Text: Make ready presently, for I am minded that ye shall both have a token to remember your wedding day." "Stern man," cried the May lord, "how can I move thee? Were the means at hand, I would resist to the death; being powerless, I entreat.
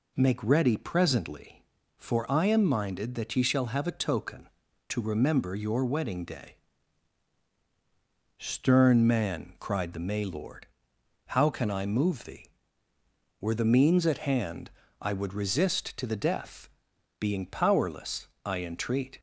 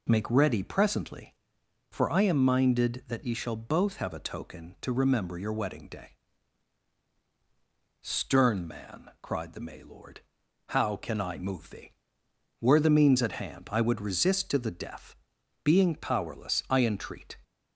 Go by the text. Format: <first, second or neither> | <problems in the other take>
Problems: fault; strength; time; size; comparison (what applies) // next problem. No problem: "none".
second | skips "both"; at 3.6 s